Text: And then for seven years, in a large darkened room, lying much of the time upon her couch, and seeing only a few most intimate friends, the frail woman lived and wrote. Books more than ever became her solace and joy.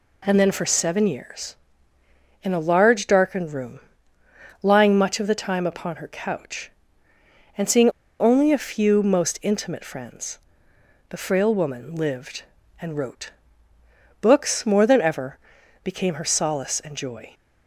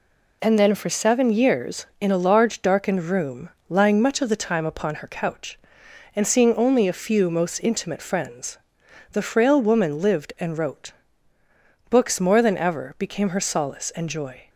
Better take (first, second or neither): second